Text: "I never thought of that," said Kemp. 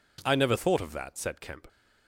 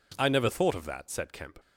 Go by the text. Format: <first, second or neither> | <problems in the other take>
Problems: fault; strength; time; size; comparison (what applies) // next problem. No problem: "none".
neither | none